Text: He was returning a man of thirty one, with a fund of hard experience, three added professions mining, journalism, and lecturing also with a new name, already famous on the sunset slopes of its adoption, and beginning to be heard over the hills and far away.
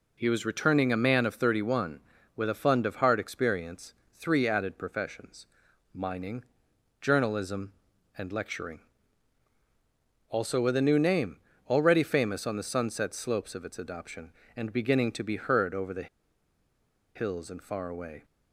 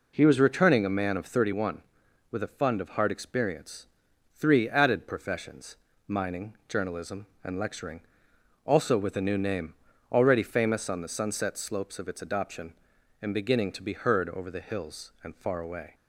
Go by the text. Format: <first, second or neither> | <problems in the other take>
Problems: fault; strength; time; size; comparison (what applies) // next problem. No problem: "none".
second | pauses between "professions" and "mining"; noticeable; at 5.4 s; 0.48 s long; slight in the second // pauses between "lecturing" and "also"; strong; at 8.8 s; 1.4 s long; noticeable in the second // pauses between "the" and "hills"; at 16.0 s; 1.0 s long